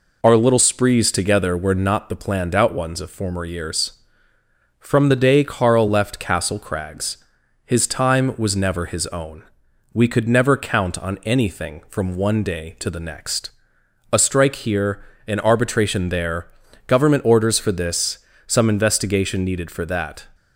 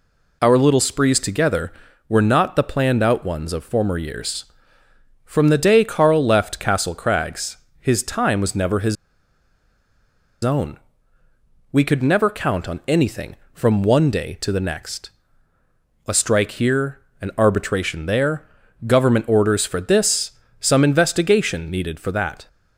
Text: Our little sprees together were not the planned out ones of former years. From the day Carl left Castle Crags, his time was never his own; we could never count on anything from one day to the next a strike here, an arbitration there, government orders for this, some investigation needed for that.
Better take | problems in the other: first | pauses between "his" and "own"; strong; at 8.9 s; 1.4 s long // pauses between "next" and "a"; noticeable; at 15.1 s; 0.96 s long; noticeable in the first

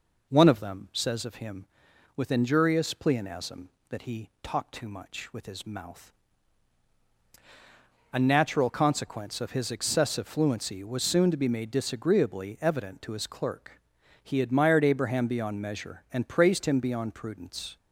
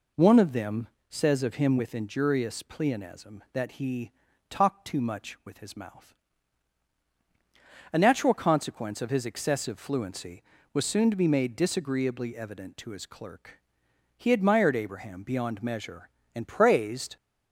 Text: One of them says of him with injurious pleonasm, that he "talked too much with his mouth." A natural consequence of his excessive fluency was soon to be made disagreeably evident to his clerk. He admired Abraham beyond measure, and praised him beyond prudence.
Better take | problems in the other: first | pauses between "them" and "says"; slight; at 0.8 s; 0.20 s long // pauses between "he" and "talked"; slight; at 4.1 s; 0.36 s long // stops before "him beyond prudence"; at 17.1 s

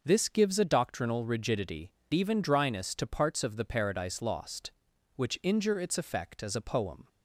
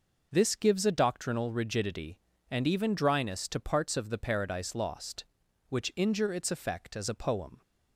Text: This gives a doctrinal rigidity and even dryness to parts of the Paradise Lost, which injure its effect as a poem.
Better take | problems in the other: second | starts louder than the rest; noticeable; until 1.0 s; 6 dB // skips "and"; at 2.0 s

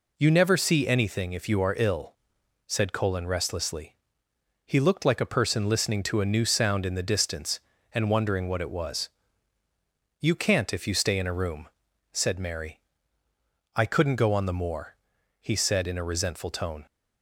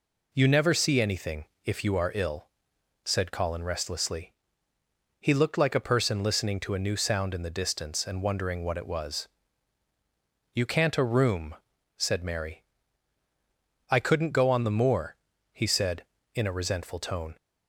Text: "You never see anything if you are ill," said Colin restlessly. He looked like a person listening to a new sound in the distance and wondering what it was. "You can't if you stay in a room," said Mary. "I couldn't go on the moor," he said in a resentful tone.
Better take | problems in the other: first | pauses between "anything" and "if"; slight; at 1.4 s; 0.20 s long // skips "if you stay in"; at 10.9 s

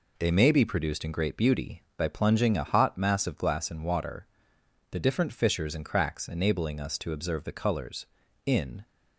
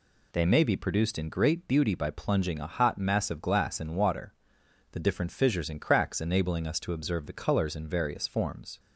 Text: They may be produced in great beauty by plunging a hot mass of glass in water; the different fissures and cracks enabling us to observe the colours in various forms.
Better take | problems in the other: second | stops before "various forms"; at 8.8 s

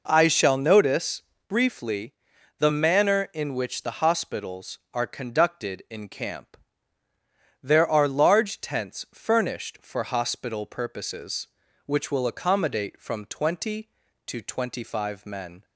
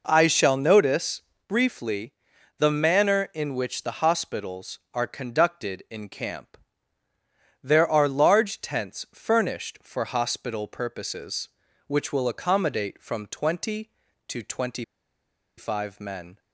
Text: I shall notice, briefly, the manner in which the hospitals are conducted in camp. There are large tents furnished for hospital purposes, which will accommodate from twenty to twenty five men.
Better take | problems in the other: first | pauses between "twenty" and "five"; noticeable; at 14.8 s; 0.73 s long

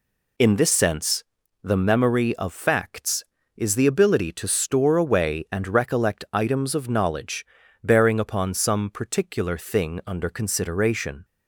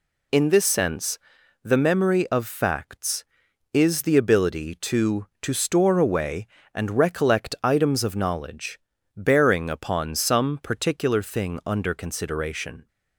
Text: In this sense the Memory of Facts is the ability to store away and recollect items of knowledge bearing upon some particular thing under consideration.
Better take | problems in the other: first | pauses between "sense" and "the"; at 1.1 s; 0.44 s long; also in the first // says "to" twice; at 5.4 s // pauses between "knowledge" and "bearing"; slight; at 8.7 s; 0.36 s long; also in the first

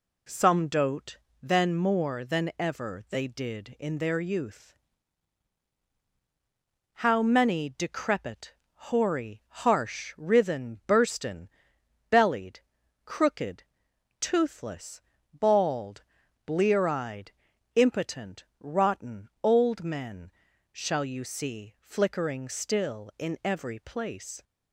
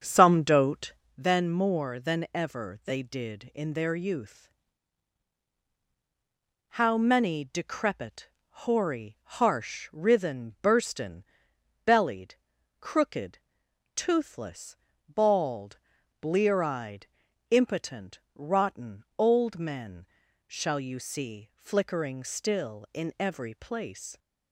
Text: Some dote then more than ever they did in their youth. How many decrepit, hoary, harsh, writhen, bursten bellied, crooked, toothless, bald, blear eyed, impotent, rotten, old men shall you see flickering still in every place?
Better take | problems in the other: first | starts louder than the rest; until 1.2 s; 7 dB // pauses between "dote" and "then"; slight; at 0.9 s; 0.22 s long; slight in the first // pauses between "bursten" and "bellied"; noticeable; at 11.2 s; 0.62 s long; noticeable in the first // pauses between "men" and "shall"; at 20.0 s; 0.44 s long; also in the first

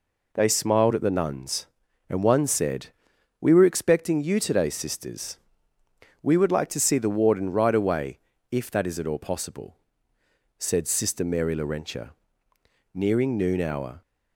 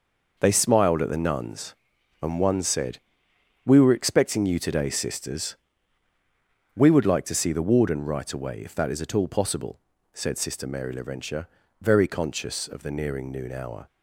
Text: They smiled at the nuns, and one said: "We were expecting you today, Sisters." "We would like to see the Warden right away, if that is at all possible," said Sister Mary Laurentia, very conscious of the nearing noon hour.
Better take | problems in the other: second | skips "very conscious of the"; at 12.5 s

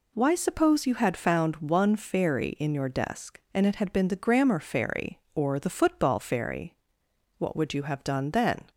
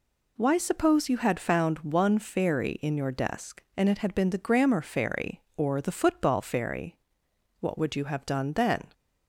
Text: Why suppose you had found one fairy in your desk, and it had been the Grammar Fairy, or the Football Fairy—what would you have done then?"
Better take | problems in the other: neither | none

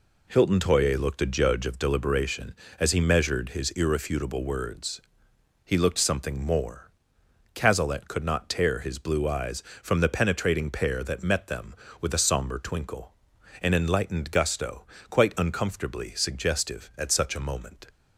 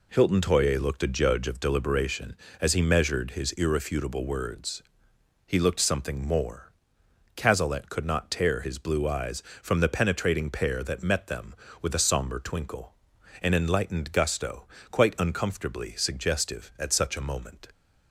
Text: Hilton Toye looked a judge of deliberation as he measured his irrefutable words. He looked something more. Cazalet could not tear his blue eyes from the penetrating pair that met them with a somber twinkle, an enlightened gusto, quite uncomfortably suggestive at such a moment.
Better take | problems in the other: neither | none

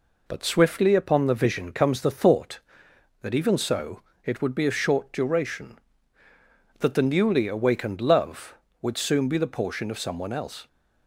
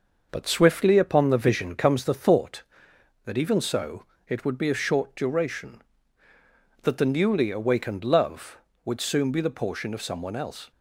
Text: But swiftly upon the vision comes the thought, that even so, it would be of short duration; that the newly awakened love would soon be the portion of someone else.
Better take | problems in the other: first | starts louder than the rest; noticeable; until 2.1 s; 6 dB

